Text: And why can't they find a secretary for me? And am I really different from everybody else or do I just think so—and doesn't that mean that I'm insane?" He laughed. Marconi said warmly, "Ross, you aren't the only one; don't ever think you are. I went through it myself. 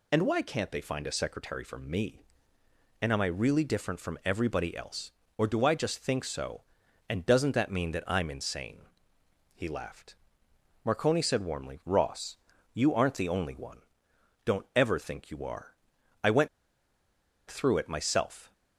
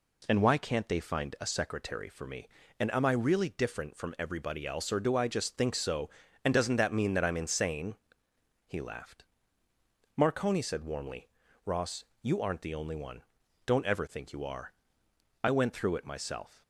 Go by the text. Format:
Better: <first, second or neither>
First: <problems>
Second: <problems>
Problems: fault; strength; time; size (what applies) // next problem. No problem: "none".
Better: second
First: pauses between "went" and "through"; at 16.4 s; 1.0 s long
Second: none